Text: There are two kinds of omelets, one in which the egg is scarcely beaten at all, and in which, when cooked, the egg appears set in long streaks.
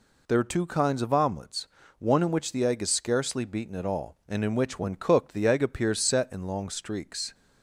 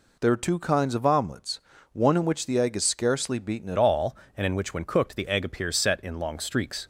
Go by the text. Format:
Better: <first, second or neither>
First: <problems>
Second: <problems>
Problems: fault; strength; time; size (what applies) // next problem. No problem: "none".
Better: first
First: none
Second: changes voice at "all"; from 3.7 s on; 3.1 s long